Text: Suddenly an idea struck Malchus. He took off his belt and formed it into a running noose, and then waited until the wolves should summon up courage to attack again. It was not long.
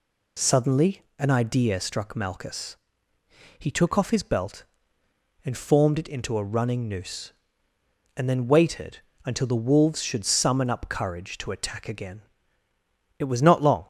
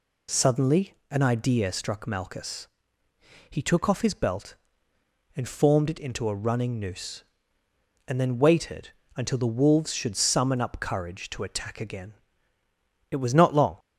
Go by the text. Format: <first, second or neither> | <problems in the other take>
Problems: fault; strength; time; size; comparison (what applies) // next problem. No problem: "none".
neither | pauses between "Suddenly" and "an"; slight; the same in both // pauses between "waited" and "until"; slight; the same in both